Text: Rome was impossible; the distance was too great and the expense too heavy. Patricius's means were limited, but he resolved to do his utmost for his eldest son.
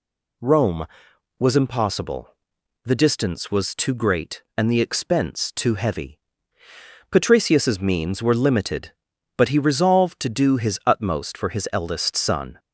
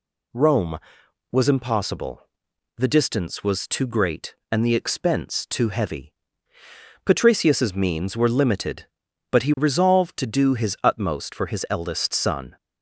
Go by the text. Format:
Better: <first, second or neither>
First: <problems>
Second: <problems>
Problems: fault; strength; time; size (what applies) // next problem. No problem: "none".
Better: neither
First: none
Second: none